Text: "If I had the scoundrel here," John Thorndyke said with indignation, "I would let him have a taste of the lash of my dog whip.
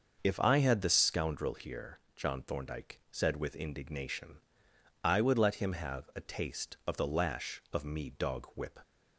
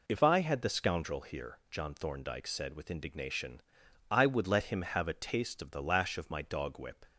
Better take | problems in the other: second | starts louder than the rest; until 1.2 s; 6 dB // says "me" for "my"; at 7.8 s

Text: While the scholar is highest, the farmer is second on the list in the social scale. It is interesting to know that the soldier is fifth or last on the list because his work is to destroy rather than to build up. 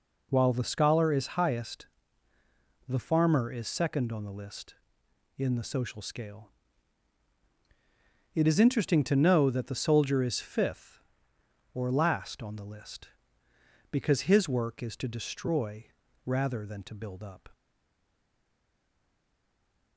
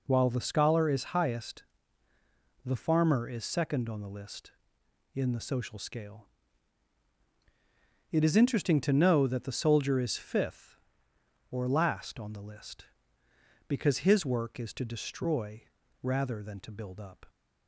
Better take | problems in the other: second | pauses between "destroy" and "rather"; at 15.8 s; 0.42 s long; also in the second // stays silent after the last word; from 17.5 s on; 2.4 s long

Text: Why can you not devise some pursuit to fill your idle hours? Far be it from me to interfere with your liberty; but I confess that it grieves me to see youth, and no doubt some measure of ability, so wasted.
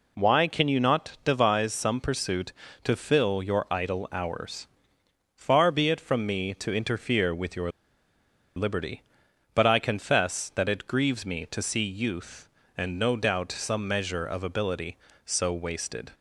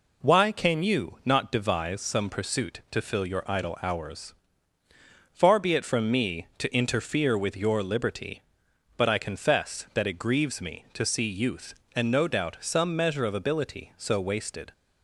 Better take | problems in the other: second | pauses between "your" and "liberty"; noticeable; at 7.6 s; 0.89 s long

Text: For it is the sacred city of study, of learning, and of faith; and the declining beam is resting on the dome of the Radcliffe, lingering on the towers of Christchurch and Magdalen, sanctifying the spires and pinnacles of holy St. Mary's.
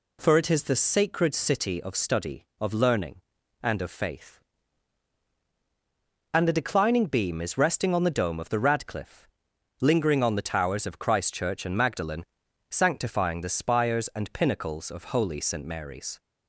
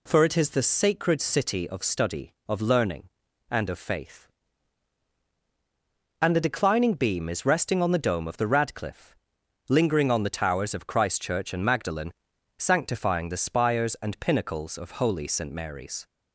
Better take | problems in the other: neither | none

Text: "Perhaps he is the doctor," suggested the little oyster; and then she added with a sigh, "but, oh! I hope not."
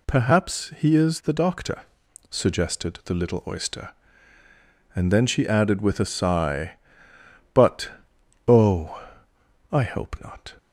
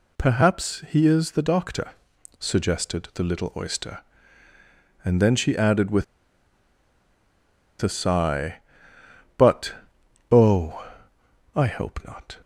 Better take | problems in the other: first | pauses between "with" and "a"; strong; at 6.0 s; 1.7 s long

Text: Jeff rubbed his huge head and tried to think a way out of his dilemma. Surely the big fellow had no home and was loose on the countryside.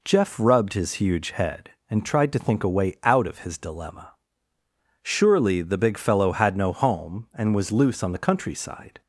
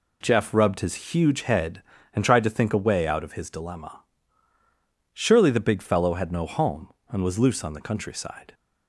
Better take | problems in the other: neither | none

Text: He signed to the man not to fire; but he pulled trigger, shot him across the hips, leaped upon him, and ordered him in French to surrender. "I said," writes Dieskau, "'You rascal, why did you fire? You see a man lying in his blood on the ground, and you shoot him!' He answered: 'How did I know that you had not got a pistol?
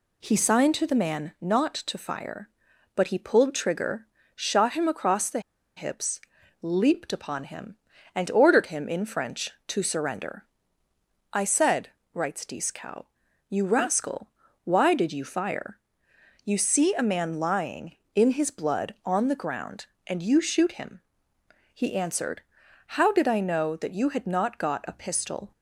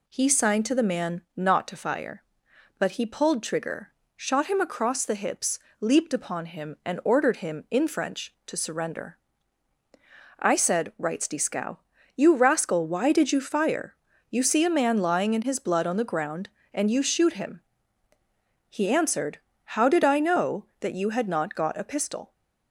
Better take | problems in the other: second | pauses between "the" and "hips"; at 5.3 s; 0.37 s long

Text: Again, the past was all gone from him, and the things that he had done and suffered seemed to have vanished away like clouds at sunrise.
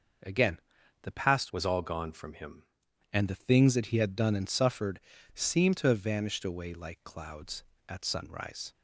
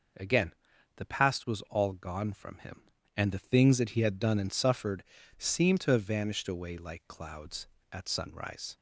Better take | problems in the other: second | changes voice from "was" to "him"; from 1.5 to 2.6 s; 1.1 s long // pauses between "suffered" and "seemed"; slight; at 4.9 s; 0.34 s long; slight in the second

